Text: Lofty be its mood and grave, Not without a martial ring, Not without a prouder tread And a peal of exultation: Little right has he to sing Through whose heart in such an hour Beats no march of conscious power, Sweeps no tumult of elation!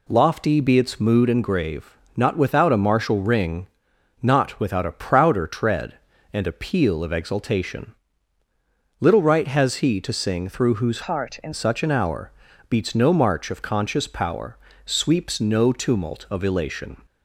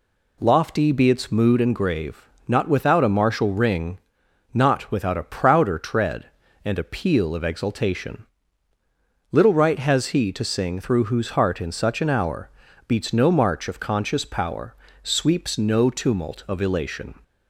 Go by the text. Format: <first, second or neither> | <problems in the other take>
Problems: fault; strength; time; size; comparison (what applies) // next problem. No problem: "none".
second | changes voice from "heart" to "in"; from 11.0 to 11.5 s; 0.5 s long // pauses between "hour" and "Beats"; at 12.3 s; 0.38 s long; also in the second